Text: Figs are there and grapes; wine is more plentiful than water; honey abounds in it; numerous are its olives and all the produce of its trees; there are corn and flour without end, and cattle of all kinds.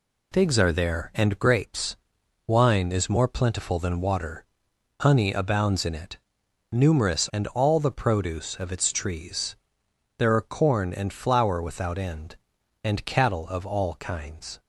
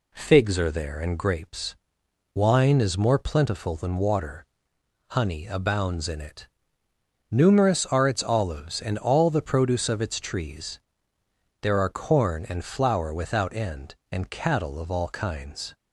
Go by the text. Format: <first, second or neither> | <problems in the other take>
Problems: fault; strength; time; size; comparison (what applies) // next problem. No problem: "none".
second | skips "are its olives"; at 7.3 s